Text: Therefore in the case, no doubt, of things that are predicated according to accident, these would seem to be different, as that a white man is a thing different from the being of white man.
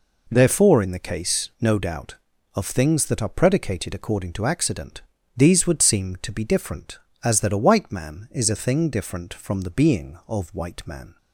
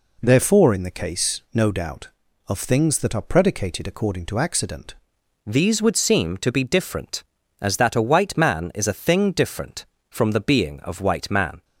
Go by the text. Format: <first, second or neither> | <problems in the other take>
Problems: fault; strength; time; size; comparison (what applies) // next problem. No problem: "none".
first | changes voice at "these"; from 5.4 s on; 6.2 s long